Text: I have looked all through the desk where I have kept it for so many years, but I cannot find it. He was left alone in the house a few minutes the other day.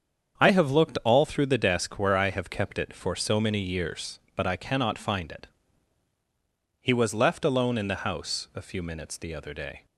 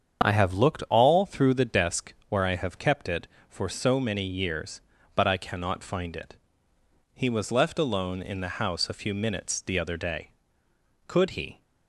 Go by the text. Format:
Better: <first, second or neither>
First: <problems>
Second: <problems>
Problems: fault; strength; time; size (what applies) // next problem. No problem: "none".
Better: first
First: starts louder than the rest; strong; until 1.4 s; 7.5 dB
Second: starts louder than the rest; strong; until 1.2 s; 7.5 dB // goes on to say "Could he"; from 11.0 s on; 0.54 s long